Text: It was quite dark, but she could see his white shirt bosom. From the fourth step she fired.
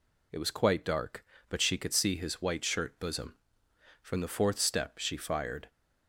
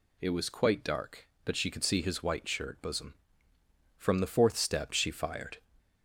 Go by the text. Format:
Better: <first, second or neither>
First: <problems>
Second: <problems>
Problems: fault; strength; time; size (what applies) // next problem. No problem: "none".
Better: neither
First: none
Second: none